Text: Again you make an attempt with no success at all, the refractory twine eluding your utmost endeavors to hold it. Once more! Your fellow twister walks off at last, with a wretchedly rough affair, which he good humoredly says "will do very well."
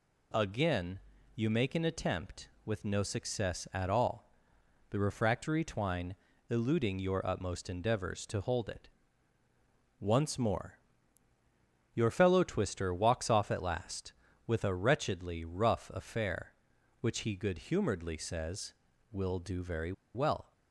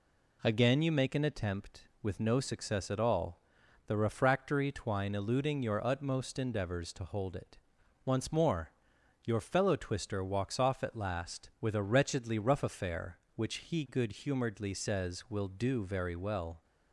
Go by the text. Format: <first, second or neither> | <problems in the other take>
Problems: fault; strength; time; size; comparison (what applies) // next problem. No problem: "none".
second | pauses between "Again" and "you"; slight; at 0.9 s; 0.36 s long // pauses between "twine" and "eluding"; slight; at 6.1 s; 0.34 s long // pauses between "very" and "well"; slight; at 19.9 s; 0.22 s long